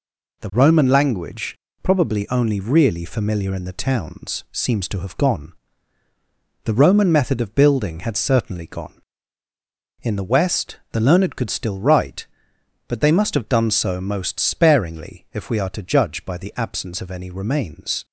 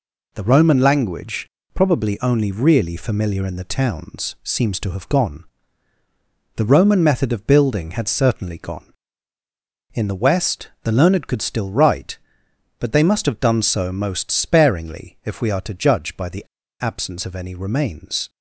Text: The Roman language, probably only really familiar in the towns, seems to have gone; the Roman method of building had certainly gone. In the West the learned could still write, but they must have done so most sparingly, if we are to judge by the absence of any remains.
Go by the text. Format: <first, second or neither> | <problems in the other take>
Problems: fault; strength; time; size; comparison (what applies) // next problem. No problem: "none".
first | pauses between "the" and "absence"; slight; at 16.4 s; 0.35 s long